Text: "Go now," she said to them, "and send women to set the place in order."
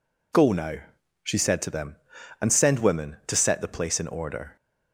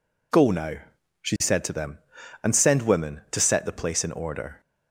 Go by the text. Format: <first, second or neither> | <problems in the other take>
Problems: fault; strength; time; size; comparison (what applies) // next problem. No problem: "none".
neither | none